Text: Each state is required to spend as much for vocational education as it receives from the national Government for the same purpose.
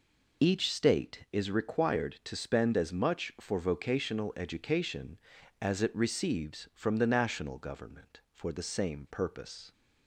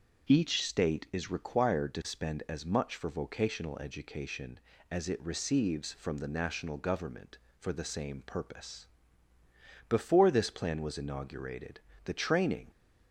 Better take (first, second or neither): first